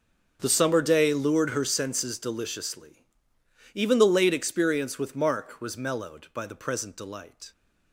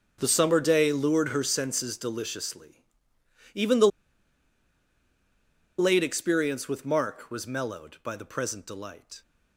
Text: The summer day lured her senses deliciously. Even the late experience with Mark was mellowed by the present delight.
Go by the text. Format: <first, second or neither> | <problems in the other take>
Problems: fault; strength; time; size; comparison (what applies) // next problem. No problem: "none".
first | starts louder than the rest; until 1.2 s; 6.5 dB; also in the first // pauses between "the" and "late"; strong; at 3.8 s; 1.9 s long